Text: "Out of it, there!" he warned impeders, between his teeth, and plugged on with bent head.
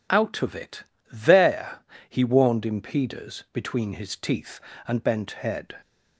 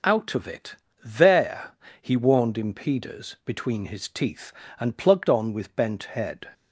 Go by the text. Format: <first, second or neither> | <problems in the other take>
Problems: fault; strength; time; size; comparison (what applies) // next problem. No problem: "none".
second | skips "plugged on with"; at 5.0 s